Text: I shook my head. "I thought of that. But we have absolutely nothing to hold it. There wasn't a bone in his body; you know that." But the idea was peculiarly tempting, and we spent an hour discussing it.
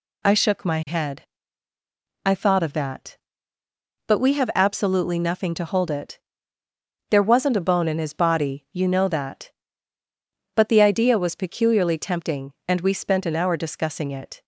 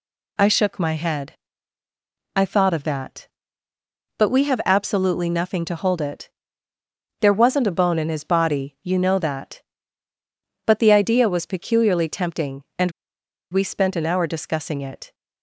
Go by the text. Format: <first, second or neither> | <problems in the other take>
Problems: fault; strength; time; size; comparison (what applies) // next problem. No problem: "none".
first | pauses between "and" and "we"; noticeable; at 12.9 s; 0.60 s long